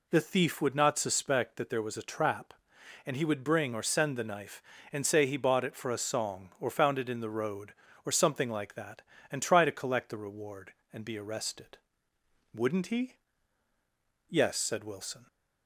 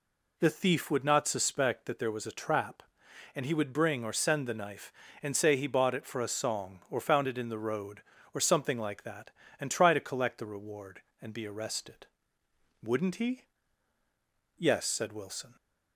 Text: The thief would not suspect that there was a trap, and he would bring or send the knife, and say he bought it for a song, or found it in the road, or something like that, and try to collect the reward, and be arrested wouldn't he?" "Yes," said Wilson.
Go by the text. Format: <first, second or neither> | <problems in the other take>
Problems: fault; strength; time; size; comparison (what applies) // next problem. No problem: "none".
neither | pauses between "arrested" and "wouldn't"; noticeable; the same in both